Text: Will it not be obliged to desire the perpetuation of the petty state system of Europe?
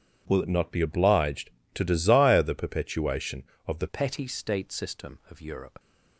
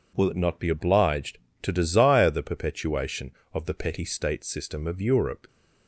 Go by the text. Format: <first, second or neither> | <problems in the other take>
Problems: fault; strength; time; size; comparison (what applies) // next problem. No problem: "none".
second | changes voice at "petty"; from 3.8 s on; 1.9 s long